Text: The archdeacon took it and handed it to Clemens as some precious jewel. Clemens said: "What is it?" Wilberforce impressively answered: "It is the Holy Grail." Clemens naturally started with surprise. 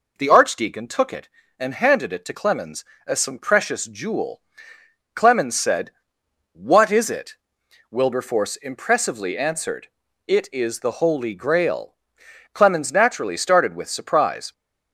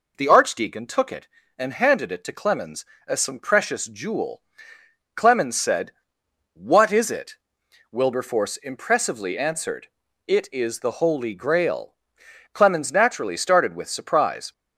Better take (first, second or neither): neither